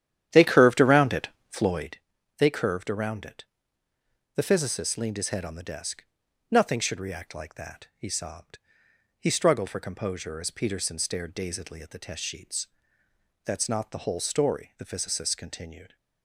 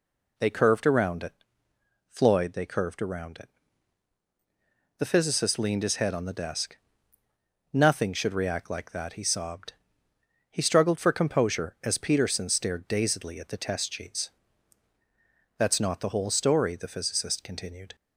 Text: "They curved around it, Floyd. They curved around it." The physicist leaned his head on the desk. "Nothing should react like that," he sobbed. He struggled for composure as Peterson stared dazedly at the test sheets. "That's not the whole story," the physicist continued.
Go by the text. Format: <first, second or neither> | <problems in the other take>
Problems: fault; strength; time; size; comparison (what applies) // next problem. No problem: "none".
second | starts louder than the rest; strong; until 2.1 s; 10.5 dB